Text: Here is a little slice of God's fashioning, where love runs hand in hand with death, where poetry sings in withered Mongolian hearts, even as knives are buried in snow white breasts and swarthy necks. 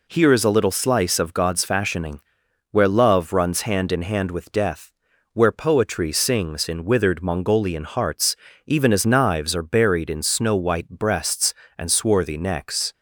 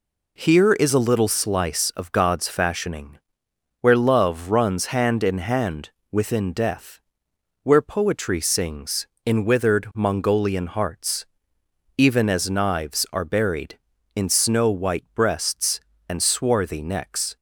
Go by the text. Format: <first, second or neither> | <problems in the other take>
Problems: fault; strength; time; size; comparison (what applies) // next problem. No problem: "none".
first | says "within" for "with"; at 6.1 s